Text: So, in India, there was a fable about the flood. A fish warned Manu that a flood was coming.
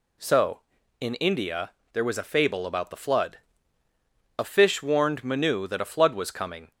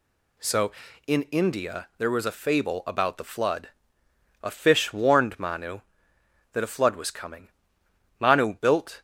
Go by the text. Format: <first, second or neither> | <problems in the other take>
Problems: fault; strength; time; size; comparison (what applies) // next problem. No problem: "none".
first | goes on to say "Manu built"; noticeable; from 8.1 s on; 0.82 s long